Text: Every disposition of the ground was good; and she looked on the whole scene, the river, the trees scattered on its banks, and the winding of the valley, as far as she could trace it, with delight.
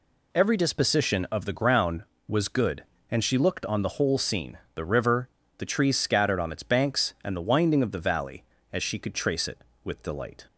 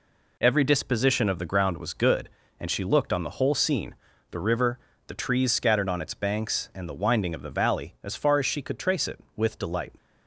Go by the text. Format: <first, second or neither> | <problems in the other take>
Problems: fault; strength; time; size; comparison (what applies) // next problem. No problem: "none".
second | skips "as far"; at 8.5 s